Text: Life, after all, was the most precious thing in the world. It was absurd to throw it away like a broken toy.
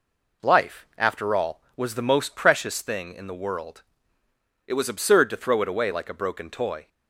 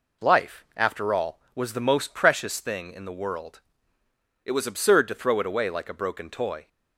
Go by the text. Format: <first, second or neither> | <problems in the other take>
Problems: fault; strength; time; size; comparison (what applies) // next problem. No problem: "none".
neither | none